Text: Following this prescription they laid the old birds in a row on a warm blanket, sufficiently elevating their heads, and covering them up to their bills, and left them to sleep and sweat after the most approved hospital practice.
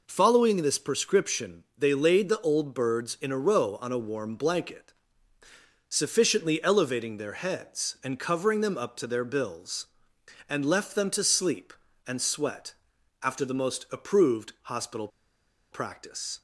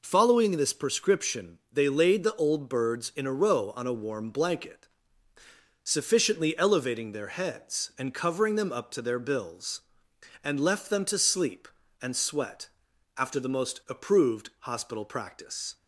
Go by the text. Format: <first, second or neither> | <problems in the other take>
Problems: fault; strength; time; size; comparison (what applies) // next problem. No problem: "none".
second | pauses between "sweat" and "after"; noticeable; at 12.7 s; 0.48 s long; noticeable in the second // pauses between "hospital" and "practice"; noticeable; at 15.0 s; 0.64 s long